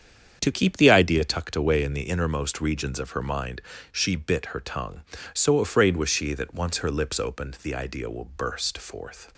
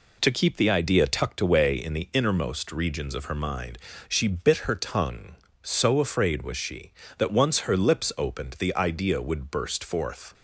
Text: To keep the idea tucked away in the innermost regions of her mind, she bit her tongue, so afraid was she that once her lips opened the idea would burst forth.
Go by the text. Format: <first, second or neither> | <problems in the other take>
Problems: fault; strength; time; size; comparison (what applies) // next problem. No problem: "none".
second | starts louder than the rest; strong; until 1.4 s; 8 dB // says "will" for "would"; at 8.0 s